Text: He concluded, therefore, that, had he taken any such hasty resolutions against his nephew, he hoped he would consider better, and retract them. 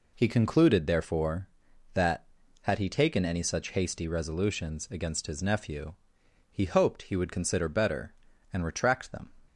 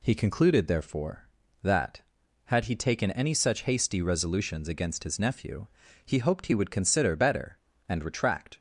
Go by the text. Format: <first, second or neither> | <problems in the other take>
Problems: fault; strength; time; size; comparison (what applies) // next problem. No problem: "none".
first | stops before "them"; at 8.5 s